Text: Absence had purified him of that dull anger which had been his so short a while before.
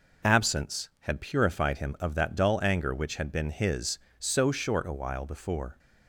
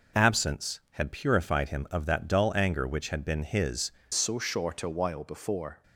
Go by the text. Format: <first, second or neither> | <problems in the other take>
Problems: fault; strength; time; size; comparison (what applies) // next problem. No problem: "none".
first | changes voice at "so"; from 4.1 s on; 1.7 s long